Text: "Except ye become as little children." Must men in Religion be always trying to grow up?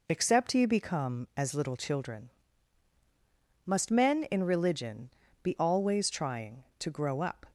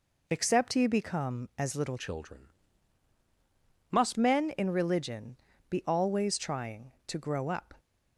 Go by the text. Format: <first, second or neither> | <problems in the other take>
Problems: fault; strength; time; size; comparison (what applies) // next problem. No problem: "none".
first | changes voice from "children" to "Must"; from 1.9 to 4.1 s; 2.2 s long // pauses between "Religion" and "be"; slight; at 5.3 s; 0.32 s long; slight in the first